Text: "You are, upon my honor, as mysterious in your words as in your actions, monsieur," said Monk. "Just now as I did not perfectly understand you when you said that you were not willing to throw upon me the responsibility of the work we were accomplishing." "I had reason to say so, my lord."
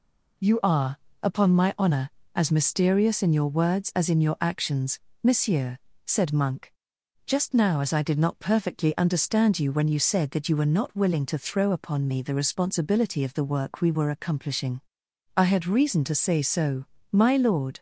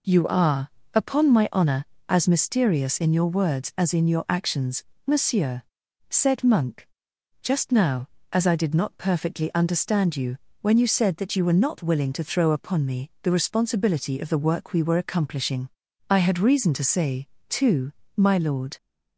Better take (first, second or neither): first